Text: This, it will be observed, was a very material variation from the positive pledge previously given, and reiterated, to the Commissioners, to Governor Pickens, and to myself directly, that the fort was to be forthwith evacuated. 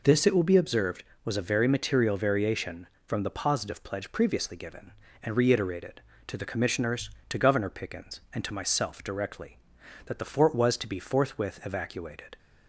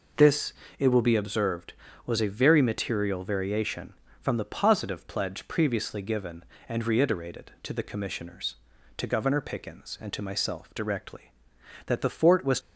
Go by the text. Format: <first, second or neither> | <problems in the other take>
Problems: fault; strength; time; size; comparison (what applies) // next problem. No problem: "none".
first | stops before "to be forthwith evacuated"; at 12.5 s